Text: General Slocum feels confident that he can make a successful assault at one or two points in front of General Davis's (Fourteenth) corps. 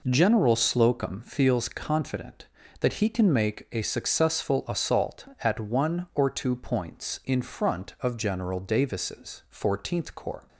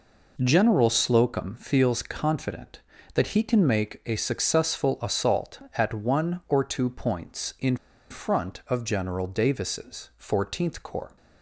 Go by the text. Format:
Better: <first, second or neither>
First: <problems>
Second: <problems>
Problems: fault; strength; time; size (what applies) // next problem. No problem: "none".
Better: first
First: none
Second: pauses between "in" and "front"; slight; at 7.7 s; 0.34 s long